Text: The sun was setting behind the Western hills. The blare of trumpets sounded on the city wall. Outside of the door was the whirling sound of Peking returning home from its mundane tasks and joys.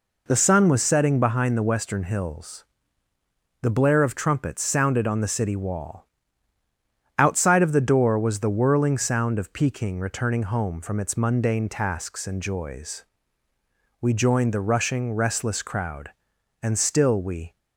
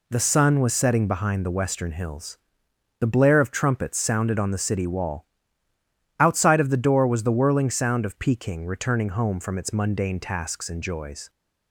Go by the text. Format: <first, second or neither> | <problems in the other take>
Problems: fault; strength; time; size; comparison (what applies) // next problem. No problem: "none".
second | goes on to say "We joined the rushing restless crowd and still we"; strong; from 14.0 s on; 3.5 s long